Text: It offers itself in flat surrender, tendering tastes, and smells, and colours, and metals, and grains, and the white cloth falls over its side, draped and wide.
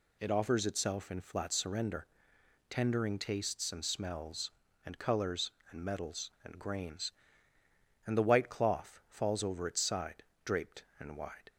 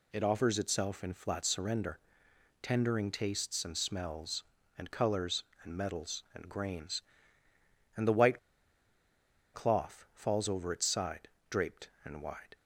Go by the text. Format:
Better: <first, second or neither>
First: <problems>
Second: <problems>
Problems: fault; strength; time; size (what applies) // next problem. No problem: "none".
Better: first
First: none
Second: pauses between "white" and "cloth"; at 8.3 s; 1.1 s long